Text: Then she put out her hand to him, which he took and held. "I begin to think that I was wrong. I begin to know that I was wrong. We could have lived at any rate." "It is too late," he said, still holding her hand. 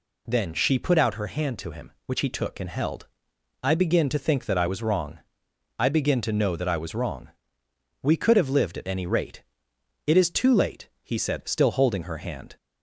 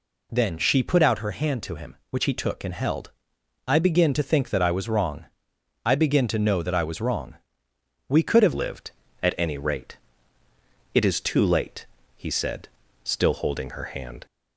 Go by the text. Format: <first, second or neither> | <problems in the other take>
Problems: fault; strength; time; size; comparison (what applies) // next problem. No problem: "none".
first | changes voice at "lived"; from 8.5 s on; 5.7 s long